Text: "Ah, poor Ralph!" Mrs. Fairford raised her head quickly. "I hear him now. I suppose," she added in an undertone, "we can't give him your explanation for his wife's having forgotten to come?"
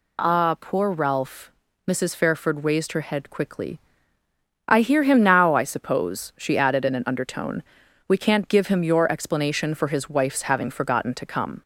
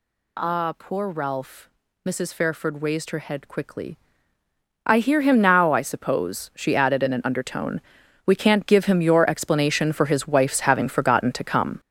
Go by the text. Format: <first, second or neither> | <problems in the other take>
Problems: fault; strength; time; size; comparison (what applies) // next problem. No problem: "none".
first | gets louder; strong; throughout; 7 dB